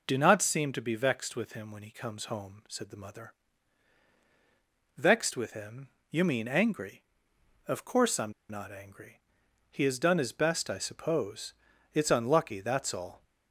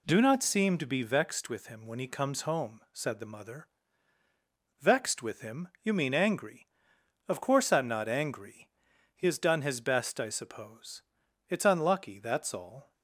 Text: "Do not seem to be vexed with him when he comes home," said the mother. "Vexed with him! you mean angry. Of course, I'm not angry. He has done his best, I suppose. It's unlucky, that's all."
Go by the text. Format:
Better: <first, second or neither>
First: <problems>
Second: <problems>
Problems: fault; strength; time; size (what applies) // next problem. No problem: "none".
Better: second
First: pauses between "I'm" and "not"; slight; at 8.3 s; 0.18 s long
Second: none